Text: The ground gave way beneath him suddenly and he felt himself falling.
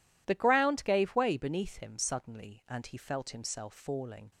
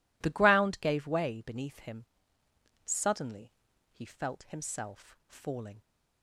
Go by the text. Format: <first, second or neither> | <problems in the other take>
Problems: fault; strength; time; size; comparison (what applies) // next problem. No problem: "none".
first | pauses between "him" and "suddenly"; noticeable; at 2.0 s; 0.80 s long // skips "and"; at 3.7 s